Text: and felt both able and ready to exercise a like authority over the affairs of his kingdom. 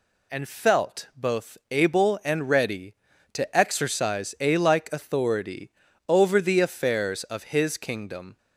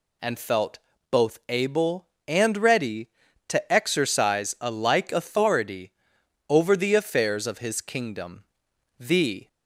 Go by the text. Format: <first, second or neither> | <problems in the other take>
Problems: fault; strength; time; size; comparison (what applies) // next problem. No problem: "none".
first | pauses between "felt" and "both"; slight; at 0.7 s; 0.32 s long // pauses between "authority" and "over"; noticeable; at 5.9 s; 0.58 s long; slight in the first // goes on to say "The"; slight; from 8.9 s on; 0.48 s long